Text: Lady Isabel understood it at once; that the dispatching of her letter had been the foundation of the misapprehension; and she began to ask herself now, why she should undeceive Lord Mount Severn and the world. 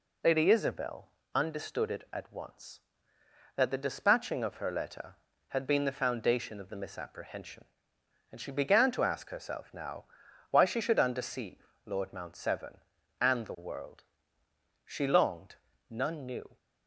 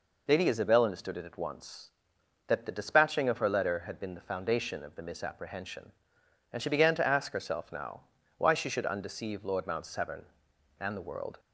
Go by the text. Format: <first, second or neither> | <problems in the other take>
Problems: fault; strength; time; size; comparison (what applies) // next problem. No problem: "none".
second | pauses between "Isabel" and "understood"; slight; at 1.0 s; 0.26 s long // pauses between "undeceive" and "Lord"; slight; at 11.6 s; 0.18 s long // goes on to say "She longed none knew"; strong; from 14.8 s on; 1.7 s long